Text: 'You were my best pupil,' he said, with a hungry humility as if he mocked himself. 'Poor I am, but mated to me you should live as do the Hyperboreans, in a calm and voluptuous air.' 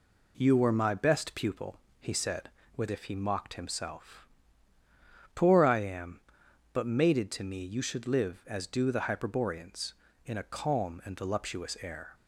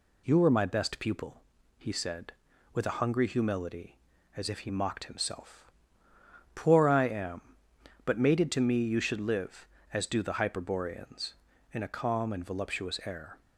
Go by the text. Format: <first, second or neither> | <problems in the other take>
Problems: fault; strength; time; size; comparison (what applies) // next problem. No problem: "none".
second | skips "a hungry humility as"; at 2.8 s